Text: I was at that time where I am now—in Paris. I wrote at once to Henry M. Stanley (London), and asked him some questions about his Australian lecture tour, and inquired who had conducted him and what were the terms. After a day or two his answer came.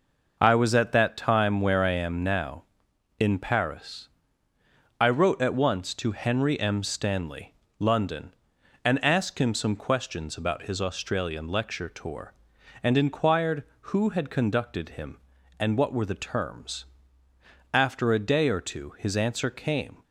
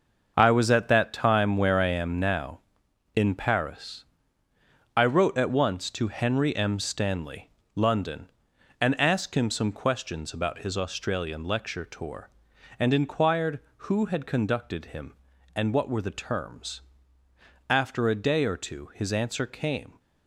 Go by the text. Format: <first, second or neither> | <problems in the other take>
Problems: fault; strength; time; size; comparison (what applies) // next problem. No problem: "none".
first | gets quieter; strong; throughout; 9.5 dB